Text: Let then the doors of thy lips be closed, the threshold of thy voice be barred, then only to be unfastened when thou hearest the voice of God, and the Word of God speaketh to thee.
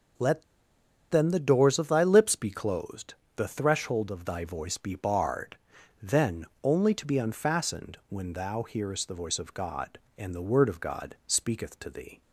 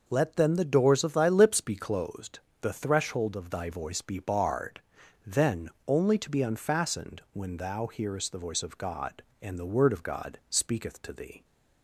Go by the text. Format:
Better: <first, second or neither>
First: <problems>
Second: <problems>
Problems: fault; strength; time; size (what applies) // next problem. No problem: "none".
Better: second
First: pauses between "Let" and "then"; noticeable; at 0.4 s; 0.66 s long // pauses between "then" and "only"; slight; at 6.4 s; 0.18 s long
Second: pauses between "then" and "only"; slight; at 5.6 s; 0.18 s long